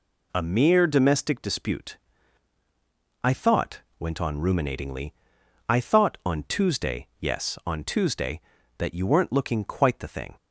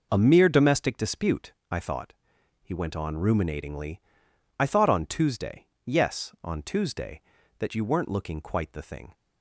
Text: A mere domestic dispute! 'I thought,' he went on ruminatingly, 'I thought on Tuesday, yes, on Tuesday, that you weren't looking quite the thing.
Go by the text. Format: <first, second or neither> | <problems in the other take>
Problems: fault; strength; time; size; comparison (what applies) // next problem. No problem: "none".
second | skips "he"; at 3.8 s